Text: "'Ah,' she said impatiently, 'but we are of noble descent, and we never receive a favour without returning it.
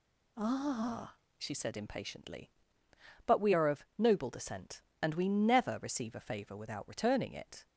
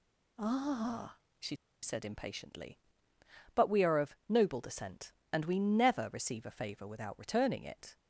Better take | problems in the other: first | pauses between "she" and "said"; slight; at 1.5 s; 0.26 s long

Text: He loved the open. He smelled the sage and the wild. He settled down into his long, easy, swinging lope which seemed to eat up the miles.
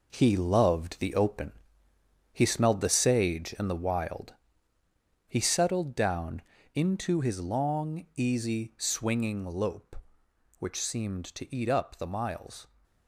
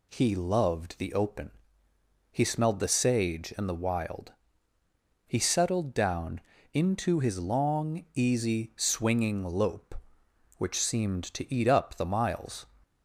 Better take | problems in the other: second | gets quieter; strong; throughout; 8.5 dB // pauses between "down" and "into"; slight; at 6.4 s; 0.34 s long; slight in the second

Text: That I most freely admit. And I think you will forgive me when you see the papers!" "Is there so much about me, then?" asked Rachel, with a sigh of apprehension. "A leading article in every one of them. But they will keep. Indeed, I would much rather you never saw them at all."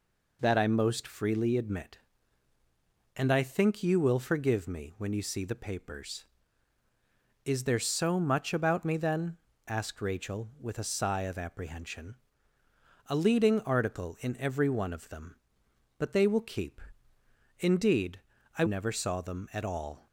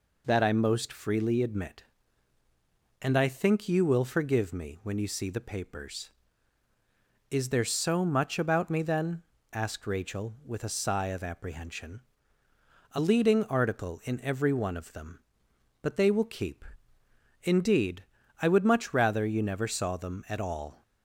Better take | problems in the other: second | skips "would much rather you"; at 18.6 s

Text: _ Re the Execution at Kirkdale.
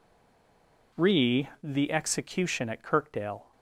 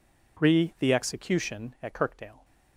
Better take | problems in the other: second | stays silent before the first word; slight; until 0.9 s; 0.9 s long

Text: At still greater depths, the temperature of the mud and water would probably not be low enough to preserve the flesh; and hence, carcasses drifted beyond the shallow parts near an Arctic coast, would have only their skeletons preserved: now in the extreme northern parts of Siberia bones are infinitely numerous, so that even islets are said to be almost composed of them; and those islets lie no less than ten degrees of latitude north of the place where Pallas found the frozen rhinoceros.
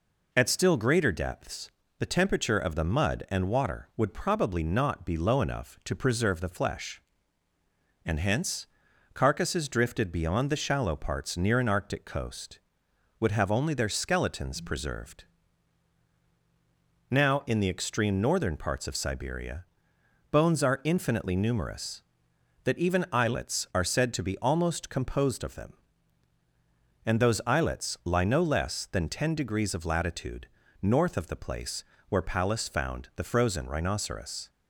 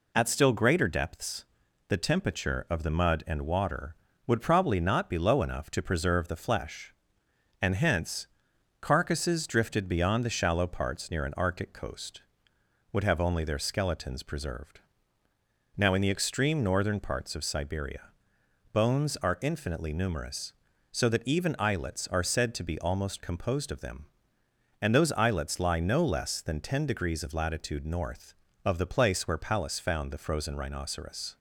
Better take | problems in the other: second | pauses between "Siberia" and "bones"; noticeable; at 19.6 s; 0.64 s long; noticeable in the second // skips "so"; at 22.3 s // pauses between "latitude" and "north"; slight; at 30.4 s; 0.36 s long // pauses between "place" and "where"; slight; at 31.8 s; 0.24 s long

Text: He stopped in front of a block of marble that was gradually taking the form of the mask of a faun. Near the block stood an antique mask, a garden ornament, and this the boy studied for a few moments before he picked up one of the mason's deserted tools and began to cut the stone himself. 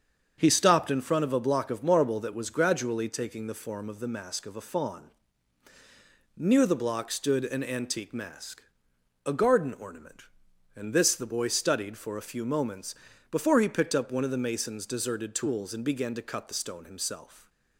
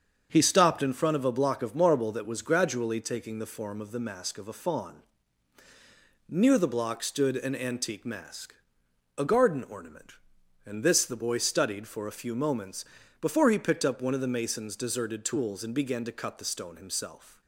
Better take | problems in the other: neither | starts louder than the rest; strong; the same in both // pauses between "moments" and "before"; slight; the same in both

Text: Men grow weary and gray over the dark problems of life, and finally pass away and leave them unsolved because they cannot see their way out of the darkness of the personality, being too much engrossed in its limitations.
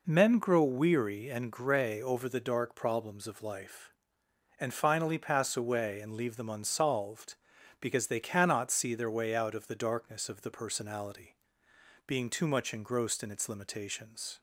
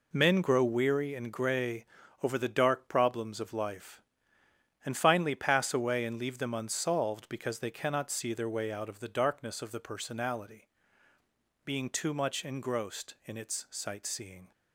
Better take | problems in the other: first | pauses between "gray" and "over"; slight; at 1.8 s; 0.36 s long // says "sightseeing" for "limitations"; at 13.7 s

